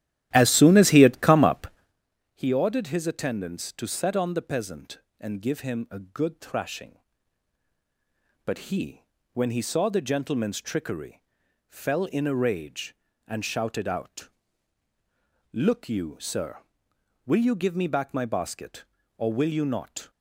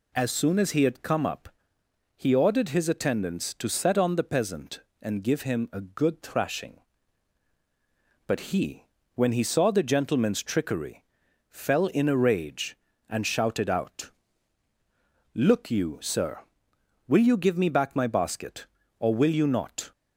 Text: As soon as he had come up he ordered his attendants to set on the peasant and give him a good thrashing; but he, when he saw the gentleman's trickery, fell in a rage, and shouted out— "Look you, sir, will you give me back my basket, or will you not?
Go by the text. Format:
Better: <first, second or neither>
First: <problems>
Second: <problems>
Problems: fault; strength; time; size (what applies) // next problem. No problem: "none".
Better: second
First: starts louder than the rest; strong; until 2.0 s; 13 dB // pauses between "up" and "he"; noticeable; at 1.6 s; 0.66 s long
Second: pauses between "up" and "he"; noticeable; at 1.4 s; 0.66 s long